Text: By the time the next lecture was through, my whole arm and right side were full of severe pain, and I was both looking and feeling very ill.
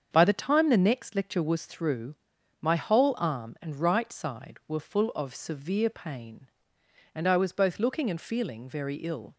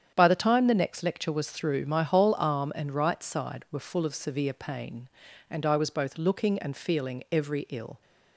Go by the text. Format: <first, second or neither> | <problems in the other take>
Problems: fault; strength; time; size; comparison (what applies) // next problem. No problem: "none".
first | starts louder than the rest; strong; until 1.1 s; 9 dB; strong in the first // says "every" for "very"; at 7.3 s